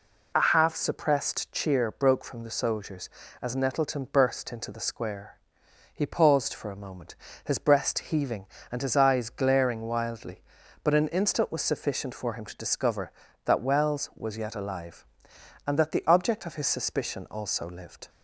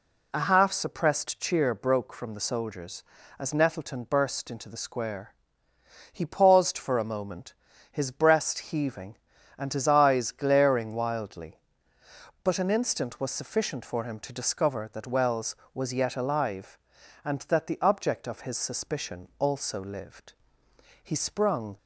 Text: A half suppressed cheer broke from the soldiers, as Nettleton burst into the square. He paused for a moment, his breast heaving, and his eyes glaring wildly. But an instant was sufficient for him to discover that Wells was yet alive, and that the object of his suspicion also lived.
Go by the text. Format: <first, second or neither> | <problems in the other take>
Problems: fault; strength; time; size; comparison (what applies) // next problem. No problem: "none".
first | goes on to say "He sprung"; noticeable; from 21.0 s on; 0.74 s long